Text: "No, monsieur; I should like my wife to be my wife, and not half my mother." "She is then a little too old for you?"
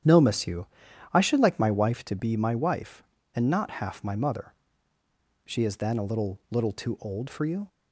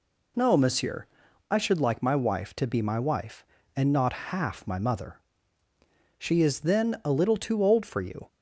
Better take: second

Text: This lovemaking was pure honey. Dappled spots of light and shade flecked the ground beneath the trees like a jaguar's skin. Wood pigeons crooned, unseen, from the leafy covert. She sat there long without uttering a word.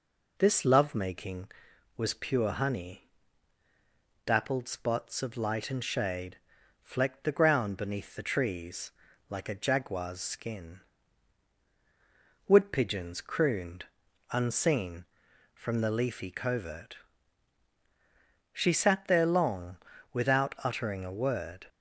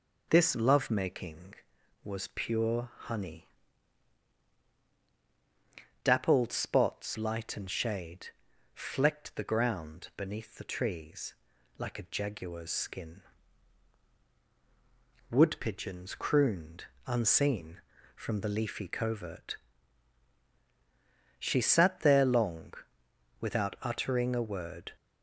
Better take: first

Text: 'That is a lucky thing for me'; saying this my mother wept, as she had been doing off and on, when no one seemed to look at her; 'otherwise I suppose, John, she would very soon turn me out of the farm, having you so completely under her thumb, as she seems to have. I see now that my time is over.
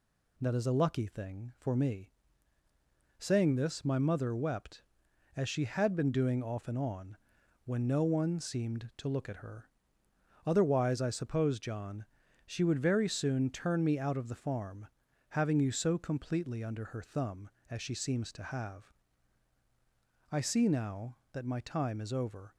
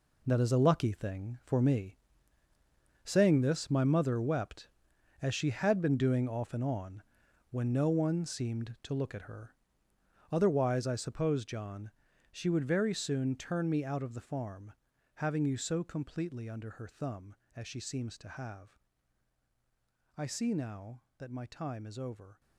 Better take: first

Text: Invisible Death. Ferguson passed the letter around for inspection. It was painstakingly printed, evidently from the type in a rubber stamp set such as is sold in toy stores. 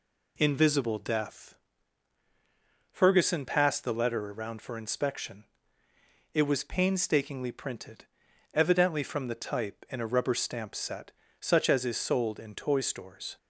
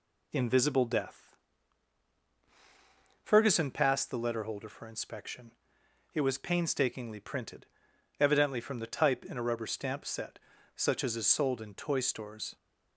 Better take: first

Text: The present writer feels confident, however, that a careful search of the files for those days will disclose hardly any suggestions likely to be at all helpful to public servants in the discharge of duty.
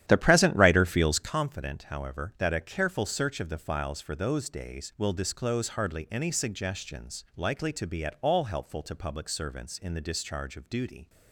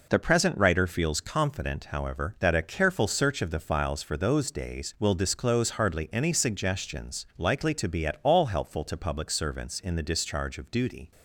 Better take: second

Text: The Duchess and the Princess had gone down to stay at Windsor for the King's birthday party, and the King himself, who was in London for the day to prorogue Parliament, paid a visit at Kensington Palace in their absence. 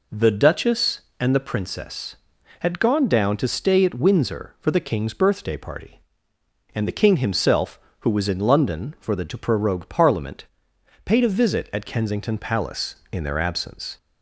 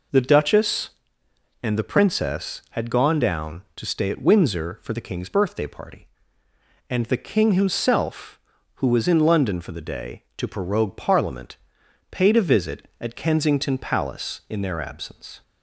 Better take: second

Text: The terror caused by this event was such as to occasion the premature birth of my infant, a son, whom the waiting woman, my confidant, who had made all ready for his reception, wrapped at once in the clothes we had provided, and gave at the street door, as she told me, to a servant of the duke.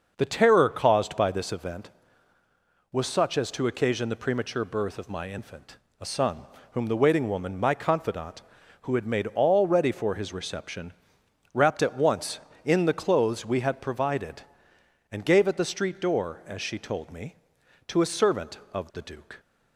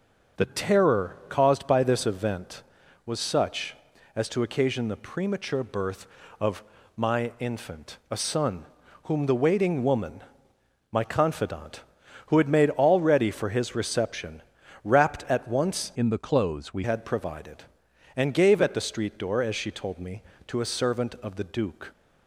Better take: first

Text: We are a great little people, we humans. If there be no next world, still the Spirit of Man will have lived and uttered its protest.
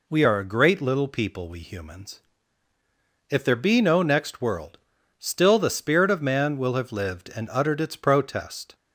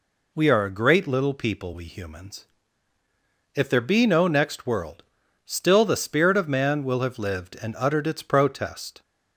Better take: neither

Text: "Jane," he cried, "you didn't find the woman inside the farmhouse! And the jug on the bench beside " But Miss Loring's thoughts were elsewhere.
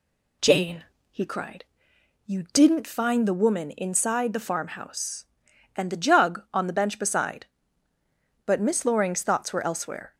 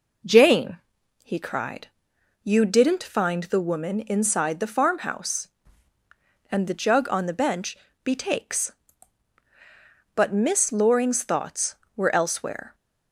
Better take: first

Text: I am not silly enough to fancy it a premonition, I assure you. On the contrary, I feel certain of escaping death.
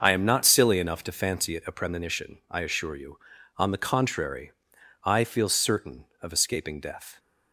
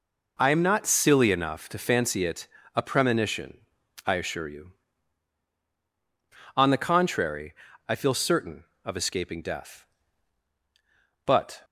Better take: first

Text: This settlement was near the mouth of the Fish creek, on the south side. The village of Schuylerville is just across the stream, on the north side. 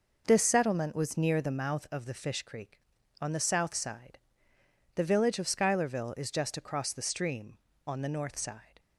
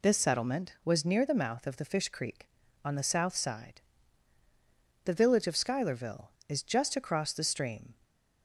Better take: first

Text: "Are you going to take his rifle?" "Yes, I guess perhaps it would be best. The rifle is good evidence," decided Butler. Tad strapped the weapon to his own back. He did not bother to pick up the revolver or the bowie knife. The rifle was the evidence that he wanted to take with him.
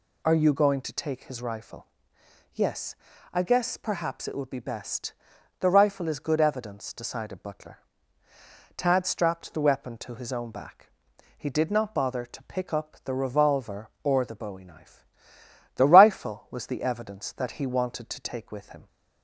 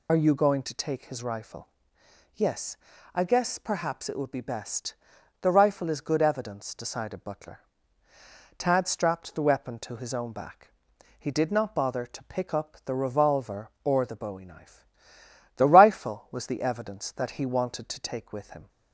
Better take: first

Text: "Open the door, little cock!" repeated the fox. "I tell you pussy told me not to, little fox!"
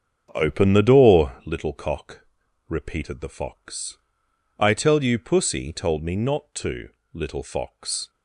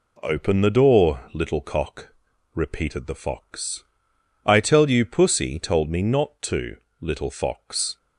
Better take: second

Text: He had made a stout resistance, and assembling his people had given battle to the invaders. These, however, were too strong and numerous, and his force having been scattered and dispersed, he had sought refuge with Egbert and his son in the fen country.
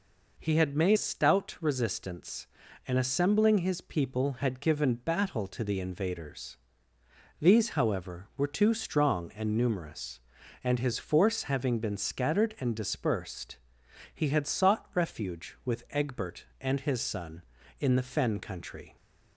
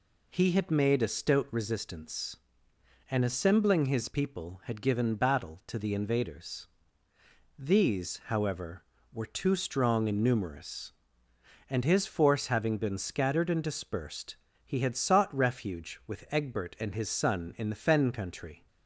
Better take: second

